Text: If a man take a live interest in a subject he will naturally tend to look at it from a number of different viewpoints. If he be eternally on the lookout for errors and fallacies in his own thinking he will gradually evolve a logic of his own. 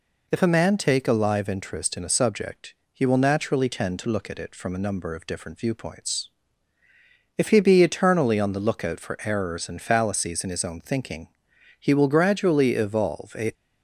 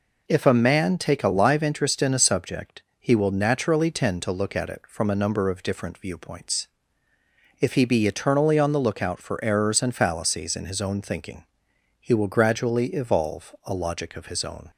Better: second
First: pauses between "subject" and "he"; slight; at 2.7 s; 0.20 s long // pauses between "thinking" and "he"; noticeable; at 11.2 s; 0.50 s long // stops before "logic of his own"; at 13.5 s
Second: pauses between "subject" and "he"; slight; at 2.8 s; 0.16 s long // pauses between "thinking" and "he"; noticeable; at 11.4 s; 0.56 s long

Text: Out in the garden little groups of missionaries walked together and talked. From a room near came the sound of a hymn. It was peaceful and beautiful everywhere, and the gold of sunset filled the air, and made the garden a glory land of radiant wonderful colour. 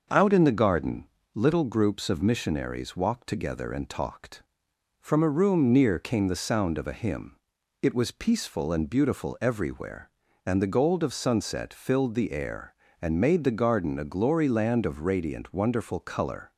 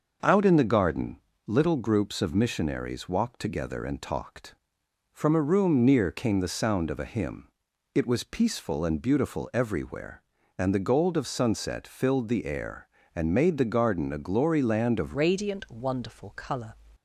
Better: first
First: pauses between "garden" and "little"; slight; at 1.0 s; 0.30 s long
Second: starts louder than the rest; noticeable; until 1.5 s; 6 dB // pauses between "garden" and "little"; slight; at 1.1 s; 0.30 s long // changes voice at "radiant"; from 15.1 s on; 1.6 s long

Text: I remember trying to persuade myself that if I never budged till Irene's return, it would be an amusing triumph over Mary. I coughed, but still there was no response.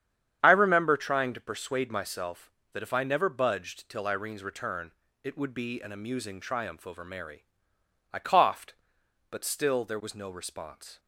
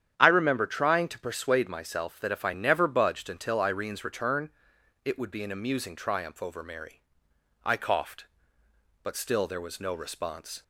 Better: first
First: starts louder than the rest; strong; until 1.4 s; 9 dB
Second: starts louder than the rest; strong; until 1.1 s; 9.5 dB // says "until" for "till"; at 3.2 s

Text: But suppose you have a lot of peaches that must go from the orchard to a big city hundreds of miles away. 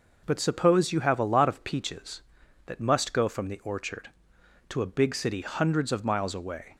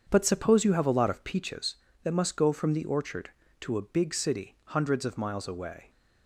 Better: first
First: none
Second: starts louder than the rest; strong; until 1.7 s; 7.5 dB

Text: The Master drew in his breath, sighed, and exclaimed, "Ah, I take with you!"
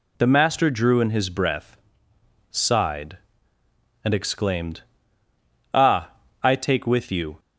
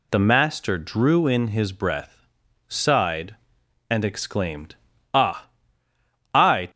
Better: first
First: none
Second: stops before "take with you"; at 6.6 s

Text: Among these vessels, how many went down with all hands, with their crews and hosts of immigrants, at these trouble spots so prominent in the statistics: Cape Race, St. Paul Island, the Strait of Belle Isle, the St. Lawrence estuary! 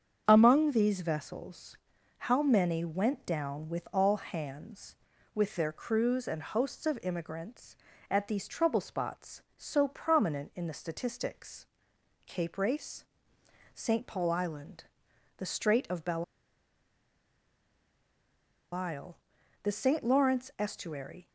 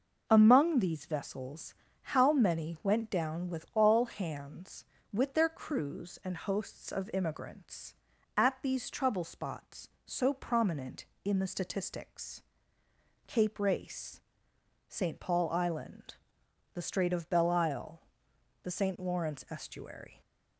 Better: second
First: starts louder than the rest; strong; until 1.2 s; 7.5 dB // pauses between "Belle" and "Isle"; strong; at 16.2 s; 2.4 s long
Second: none

